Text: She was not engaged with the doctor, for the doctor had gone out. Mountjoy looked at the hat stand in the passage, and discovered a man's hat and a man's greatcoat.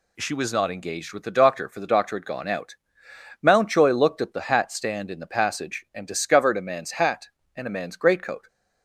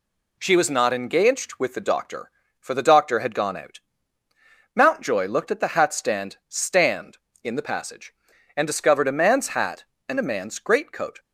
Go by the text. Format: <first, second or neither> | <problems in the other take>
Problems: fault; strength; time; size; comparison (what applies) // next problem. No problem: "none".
first | says "stand" twice; at 6.4 s